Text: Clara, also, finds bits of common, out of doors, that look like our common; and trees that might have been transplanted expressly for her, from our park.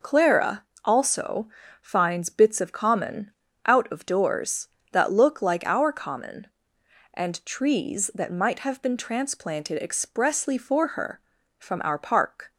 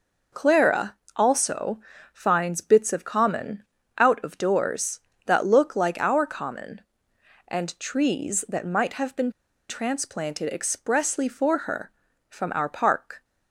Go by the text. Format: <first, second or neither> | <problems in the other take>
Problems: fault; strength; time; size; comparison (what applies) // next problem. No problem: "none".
first | pauses between "been" and "transplanted"; at 9.2 s; 0.39 s long